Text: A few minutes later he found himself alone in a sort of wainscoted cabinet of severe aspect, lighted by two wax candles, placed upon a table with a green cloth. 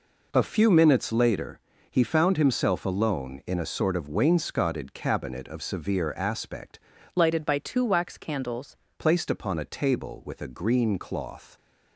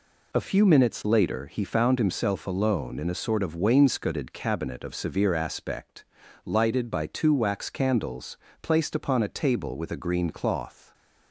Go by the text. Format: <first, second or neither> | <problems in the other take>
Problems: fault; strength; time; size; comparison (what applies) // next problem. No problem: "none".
second | pauses between "later" and "he"; slight; at 1.5 s; 0.32 s long // changes voice from "lighted" to "candles"; from 7.1 to 8.7 s; 1.6 s long